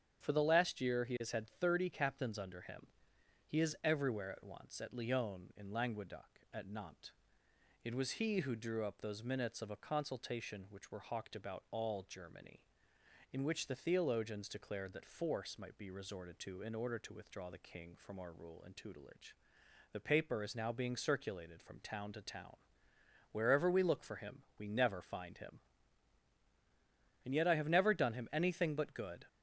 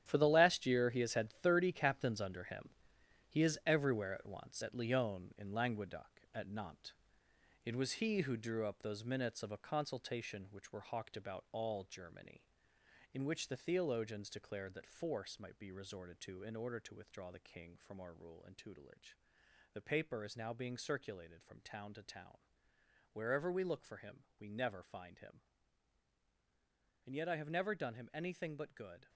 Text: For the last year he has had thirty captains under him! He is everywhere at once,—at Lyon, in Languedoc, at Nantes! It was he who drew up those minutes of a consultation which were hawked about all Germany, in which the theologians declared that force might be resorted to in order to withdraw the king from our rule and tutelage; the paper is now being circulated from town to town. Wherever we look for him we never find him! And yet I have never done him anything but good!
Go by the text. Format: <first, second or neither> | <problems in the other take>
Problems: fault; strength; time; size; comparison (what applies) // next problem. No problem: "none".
first | gets quieter; strong; throughout; 10 dB // starts louder than the rest; strong; until 1.0 s; 10.5 dB; strong in the first // pauses between "him" and "we"; slight; at 24.1 s; 0.18 s long; slight in the first